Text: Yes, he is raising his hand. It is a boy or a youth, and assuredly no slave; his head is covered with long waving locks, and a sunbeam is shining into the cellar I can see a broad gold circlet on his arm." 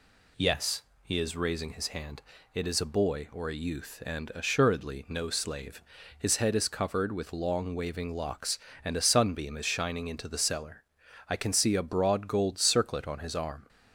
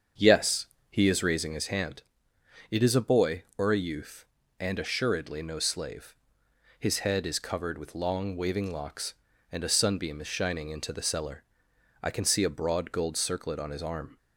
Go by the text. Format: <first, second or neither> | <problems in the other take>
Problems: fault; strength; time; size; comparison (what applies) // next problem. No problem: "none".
first | starts louder than the rest; until 1.7 s; 7 dB // pauses between "cellar" and "I"; noticeable; at 11.4 s; 0.60 s long; noticeable in the first